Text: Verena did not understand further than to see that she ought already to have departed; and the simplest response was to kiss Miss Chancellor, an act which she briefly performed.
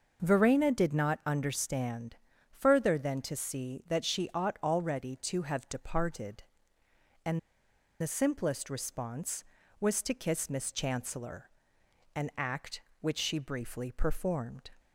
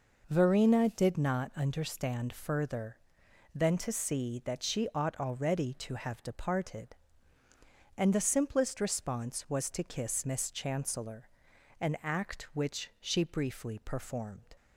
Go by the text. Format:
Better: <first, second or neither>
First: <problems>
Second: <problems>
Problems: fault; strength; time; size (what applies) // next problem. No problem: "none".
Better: second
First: pauses between "understand" and "further"; at 2.1 s; 0.38 s long // pauses between "and" and "the"; noticeable; at 7.3 s; 0.61 s long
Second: none